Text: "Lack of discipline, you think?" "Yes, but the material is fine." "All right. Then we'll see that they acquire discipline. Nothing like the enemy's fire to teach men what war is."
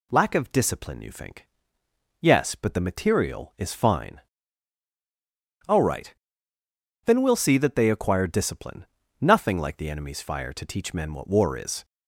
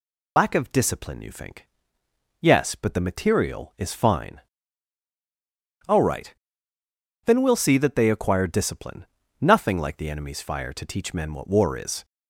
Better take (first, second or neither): first